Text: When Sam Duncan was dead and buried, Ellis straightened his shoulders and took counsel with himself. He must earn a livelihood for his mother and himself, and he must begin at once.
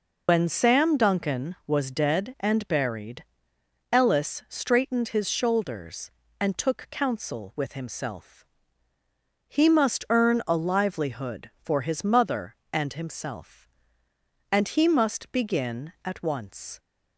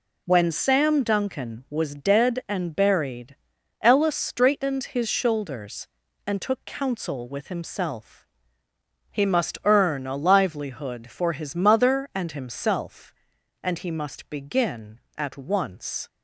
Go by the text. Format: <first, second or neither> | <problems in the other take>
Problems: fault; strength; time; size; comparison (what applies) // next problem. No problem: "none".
second | loses the start of "When"; at 0.2 s; 120 ms